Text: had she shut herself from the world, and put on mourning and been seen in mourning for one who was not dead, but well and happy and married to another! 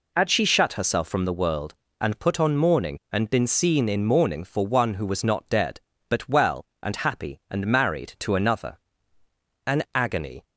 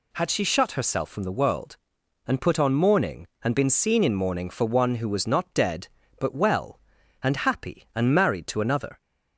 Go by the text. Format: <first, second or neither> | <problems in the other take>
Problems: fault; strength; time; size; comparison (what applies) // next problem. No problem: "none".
second | goes on to say "An agony"; noticeable; from 9.6 s on; 0.78 s long